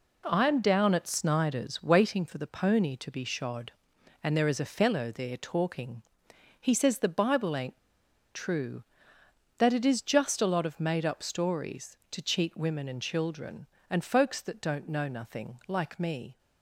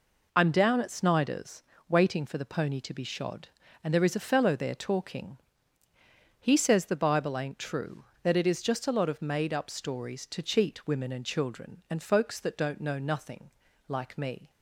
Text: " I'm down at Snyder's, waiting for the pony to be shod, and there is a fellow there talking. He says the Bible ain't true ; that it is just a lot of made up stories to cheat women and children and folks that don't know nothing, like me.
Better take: second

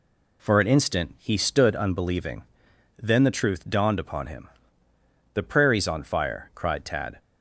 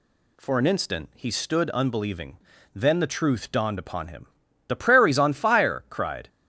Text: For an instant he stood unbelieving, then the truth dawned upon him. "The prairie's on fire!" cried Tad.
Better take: first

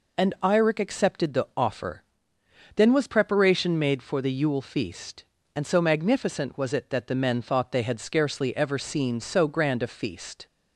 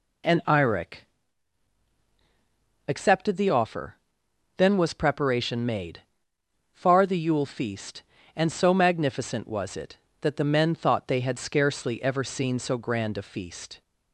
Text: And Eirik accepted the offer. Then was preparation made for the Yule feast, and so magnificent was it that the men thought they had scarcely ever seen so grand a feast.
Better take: first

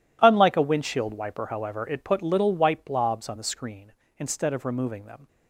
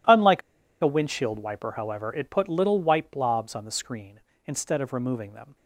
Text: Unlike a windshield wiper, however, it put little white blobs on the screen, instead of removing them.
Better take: first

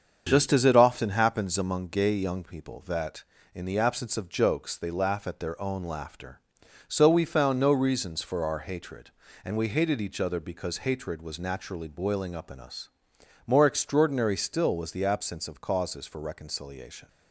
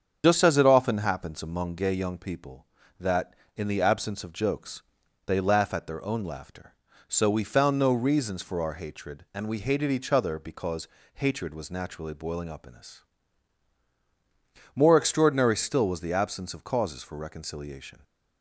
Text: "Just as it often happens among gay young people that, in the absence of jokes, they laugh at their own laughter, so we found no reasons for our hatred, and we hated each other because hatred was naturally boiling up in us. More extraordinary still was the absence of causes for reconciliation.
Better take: first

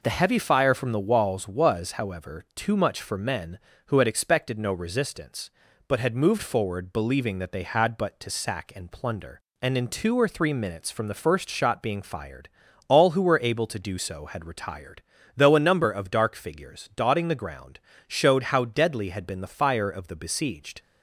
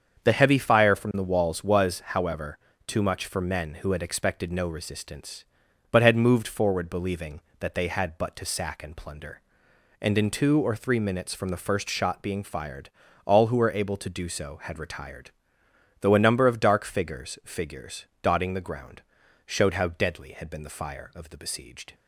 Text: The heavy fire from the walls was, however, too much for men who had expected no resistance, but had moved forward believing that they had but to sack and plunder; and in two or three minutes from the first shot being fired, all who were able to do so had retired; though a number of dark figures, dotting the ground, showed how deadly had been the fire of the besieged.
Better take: first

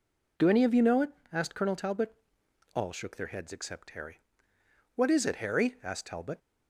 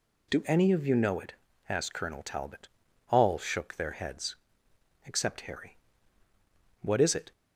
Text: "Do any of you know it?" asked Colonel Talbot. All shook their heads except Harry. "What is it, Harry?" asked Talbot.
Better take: first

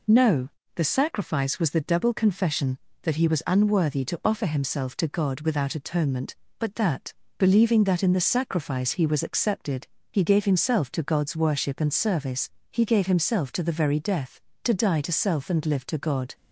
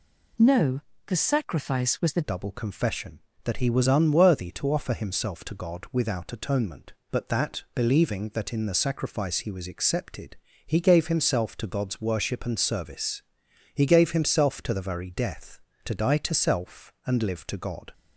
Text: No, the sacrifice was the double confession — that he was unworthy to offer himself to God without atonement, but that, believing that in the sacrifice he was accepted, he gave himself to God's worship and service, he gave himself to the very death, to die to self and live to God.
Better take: first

